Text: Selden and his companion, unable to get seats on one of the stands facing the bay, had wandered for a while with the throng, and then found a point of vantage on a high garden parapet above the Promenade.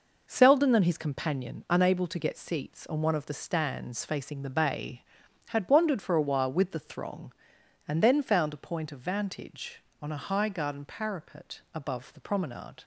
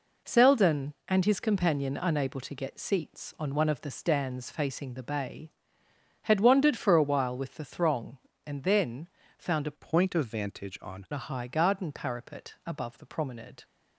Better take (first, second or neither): first